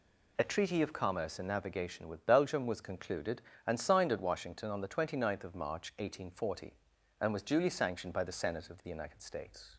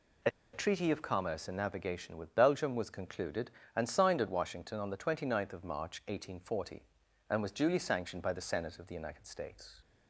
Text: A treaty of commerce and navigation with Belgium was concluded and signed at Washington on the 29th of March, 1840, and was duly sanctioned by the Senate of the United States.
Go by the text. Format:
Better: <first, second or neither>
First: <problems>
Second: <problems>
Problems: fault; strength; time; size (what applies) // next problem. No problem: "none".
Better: first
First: none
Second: pauses between "A" and "treaty"; slight; at 0.3 s; 0.23 s long